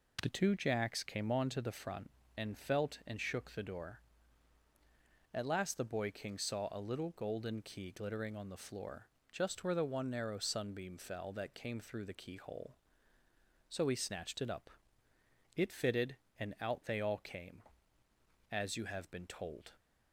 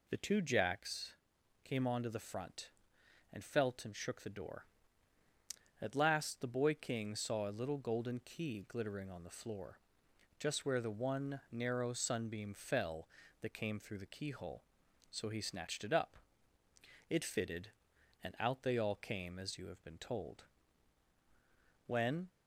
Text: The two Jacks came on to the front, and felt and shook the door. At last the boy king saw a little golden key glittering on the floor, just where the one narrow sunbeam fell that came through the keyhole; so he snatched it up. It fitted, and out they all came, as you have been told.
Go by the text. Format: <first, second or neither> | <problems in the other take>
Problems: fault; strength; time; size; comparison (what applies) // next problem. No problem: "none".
first | pauses between "Jacks" and "came"; noticeable; at 1.1 s; 0.50 s long // goes on to say "When"; slight; from 21.8 s on; 0.42 s long